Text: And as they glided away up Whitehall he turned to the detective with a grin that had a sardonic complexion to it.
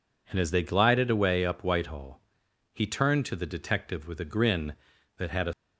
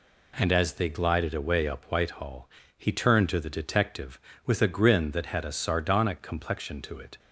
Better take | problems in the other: second | pauses between "Whitehall" and "he"; noticeable; at 2.1 s; 0.54 s long; slight in the second // stops before "sardonic complexion to it"; at 5.5 s

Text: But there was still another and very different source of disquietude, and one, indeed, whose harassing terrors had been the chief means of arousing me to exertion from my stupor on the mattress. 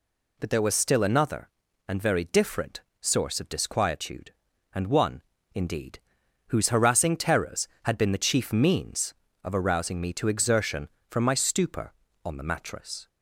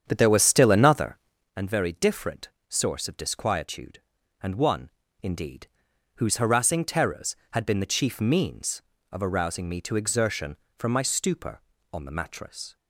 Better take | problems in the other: first | starts louder than the rest; strong; until 1.5 s; 8 dB // pauses between "different" and "source"; slight; at 2.4 s; 0.18 s long; slight in the first

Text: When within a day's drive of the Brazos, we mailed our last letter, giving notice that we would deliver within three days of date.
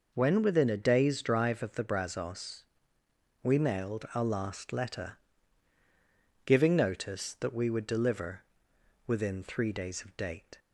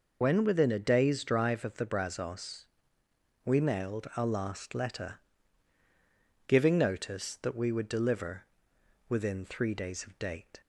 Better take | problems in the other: first | loses the start of "When"; at 0.2 s; 40 ms // pauses between "deliver" and "within"; noticeable; at 8.4 s; 0.64 s long; noticeable in the first

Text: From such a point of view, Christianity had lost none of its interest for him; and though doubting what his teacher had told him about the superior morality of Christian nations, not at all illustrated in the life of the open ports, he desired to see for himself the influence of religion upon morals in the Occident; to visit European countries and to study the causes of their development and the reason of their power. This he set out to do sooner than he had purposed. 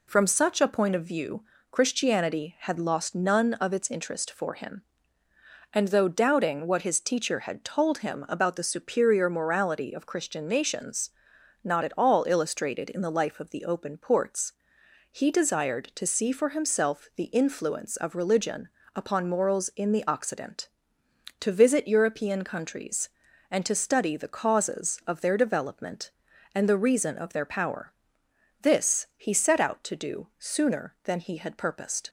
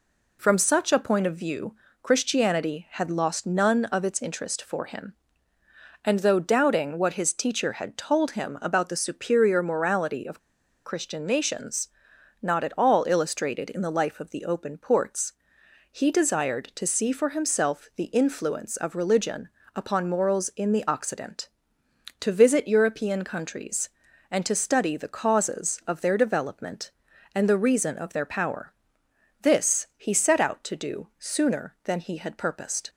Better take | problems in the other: first | pauses between "of" and "Christian"; noticeable; at 10.3 s; 0.46 s long // pauses between "religion" and "upon"; slight; at 19.4 s; 0.26 s long; slight in the first

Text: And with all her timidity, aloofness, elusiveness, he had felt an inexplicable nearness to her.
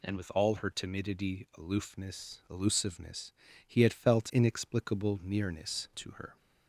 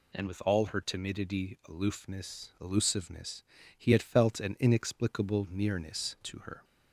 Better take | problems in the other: second | skips "an"; at 4.3 s

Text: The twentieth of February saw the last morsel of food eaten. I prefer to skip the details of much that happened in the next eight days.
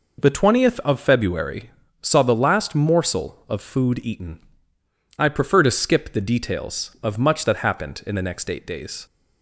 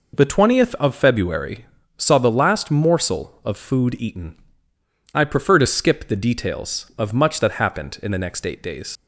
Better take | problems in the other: first | pauses between "February" and "saw"; slight; at 1.6 s; 0.32 s long; slight in the first // leaves "days" unfinished; at 8.9 s; 65 ms

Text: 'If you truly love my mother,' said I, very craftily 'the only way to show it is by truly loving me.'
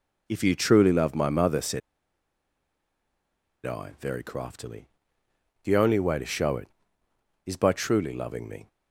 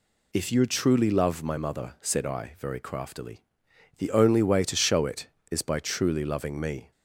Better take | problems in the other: second | pauses between "said" and "I"; strong; at 1.8 s; 1.8 s long // pauses between "craftily" and "the"; noticeable; at 4.8 s; 0.76 s long; noticeable in the second

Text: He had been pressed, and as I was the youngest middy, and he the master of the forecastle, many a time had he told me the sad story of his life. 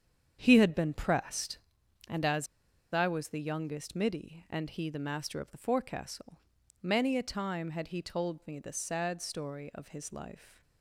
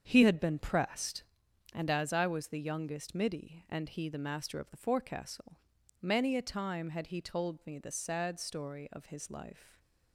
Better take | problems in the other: second | starts louder than the rest; strong; until 1.4 s; 8 dB; strong in the second // pauses between "as" and "I"; noticeable; at 2.4 s; 0.47 s long

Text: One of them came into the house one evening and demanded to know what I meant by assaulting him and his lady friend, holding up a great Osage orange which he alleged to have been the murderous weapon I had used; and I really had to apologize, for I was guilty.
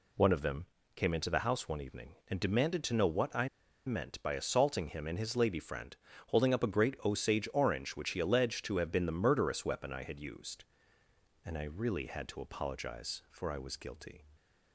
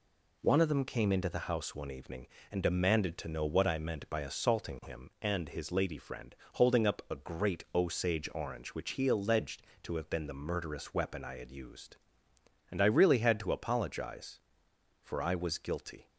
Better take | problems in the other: second | pauses between "them" and "came"; slight; at 0.6 s; 0.30 s long // pauses between "I" and "meant"; at 3.4 s; 0.38 s long

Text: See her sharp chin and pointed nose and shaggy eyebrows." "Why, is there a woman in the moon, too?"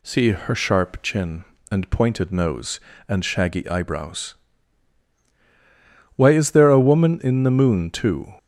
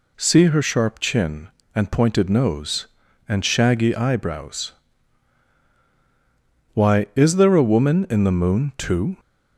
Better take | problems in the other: neither | none

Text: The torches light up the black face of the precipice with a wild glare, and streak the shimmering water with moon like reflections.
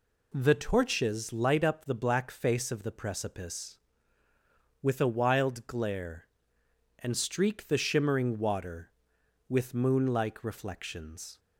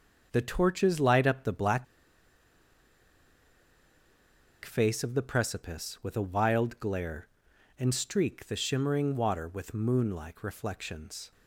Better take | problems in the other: first | starts louder than the rest; until 1.3 s; 6.5 dB // pauses between "black" and "face"; strong; at 1.8 s; 2.7 s long

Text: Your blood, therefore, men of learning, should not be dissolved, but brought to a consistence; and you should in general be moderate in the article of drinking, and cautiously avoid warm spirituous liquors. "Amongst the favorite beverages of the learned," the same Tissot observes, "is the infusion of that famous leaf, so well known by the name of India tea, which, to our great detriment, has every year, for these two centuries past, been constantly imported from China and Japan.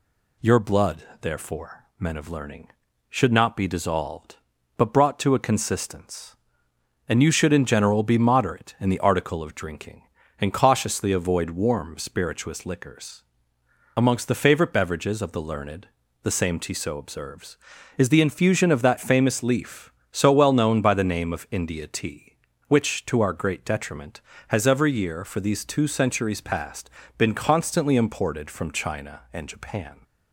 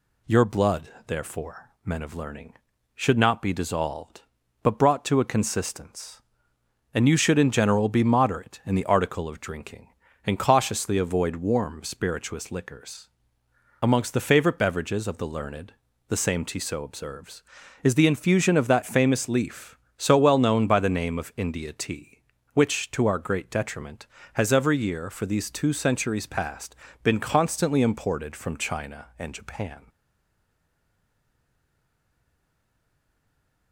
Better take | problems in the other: first | stays silent after the last word; strong; from 29.8 s on; 3.9 s long

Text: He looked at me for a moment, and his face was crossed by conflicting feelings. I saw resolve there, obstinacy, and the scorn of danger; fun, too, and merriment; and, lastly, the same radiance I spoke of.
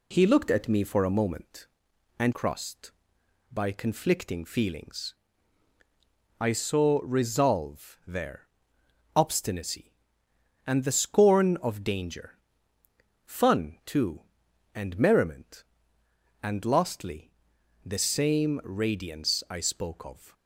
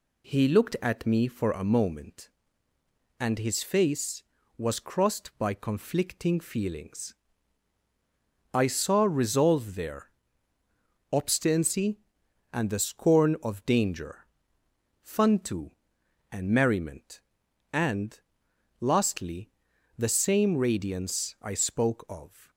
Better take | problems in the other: second | skips "his face was"; at 2.3 s

